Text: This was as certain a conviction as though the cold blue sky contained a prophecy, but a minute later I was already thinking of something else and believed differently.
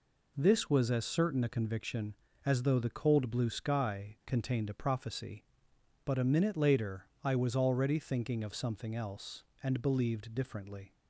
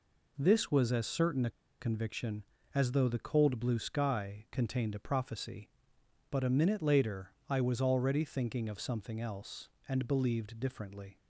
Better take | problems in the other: first | pauses between "a" and "conviction"; slight; at 1.4 s; 0.30 s long // pauses between "later" and "I"; slight; at 7.3 s; 0.18 s long; slight in the first

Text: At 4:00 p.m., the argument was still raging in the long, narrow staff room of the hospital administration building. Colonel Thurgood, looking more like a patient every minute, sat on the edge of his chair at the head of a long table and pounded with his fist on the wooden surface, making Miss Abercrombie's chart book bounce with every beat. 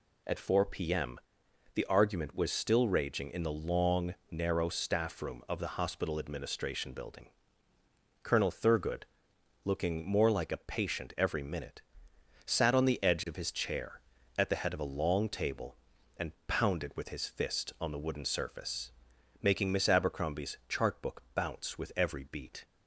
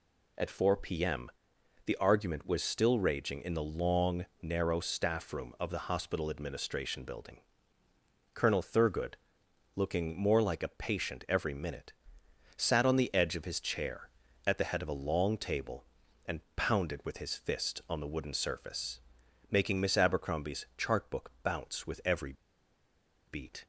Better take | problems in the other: first | pauses between "and" and "pounded"; slight; at 16.4 s; 0.16 s long; slight in the first // pauses between "every" and "beat"; noticeable; at 22.3 s; 0.94 s long

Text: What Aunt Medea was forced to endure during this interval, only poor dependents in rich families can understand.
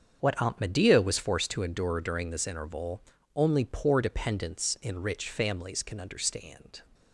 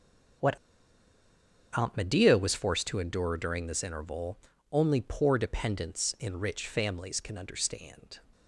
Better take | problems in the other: first | starts louder than the rest; strong; until 2.6 s; 7 dB; strong in the first // pauses between "What" and "Aunt"; at 0.5 s; 1.1 s long

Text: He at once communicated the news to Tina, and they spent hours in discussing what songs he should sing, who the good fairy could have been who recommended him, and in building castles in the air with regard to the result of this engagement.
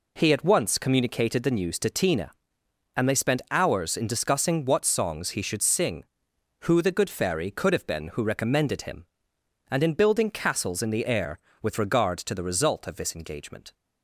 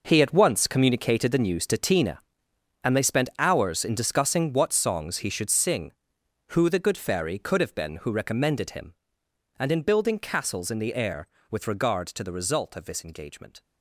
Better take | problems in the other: first | gets quieter; strong; throughout; 11.5 dB

